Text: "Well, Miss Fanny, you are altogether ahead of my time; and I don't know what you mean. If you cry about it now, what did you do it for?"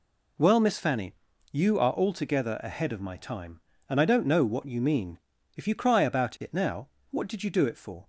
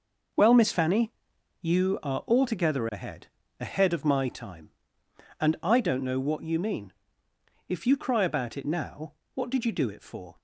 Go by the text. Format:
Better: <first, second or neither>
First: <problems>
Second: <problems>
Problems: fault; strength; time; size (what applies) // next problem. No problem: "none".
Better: first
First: none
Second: says "ahead" twice; at 3.5 s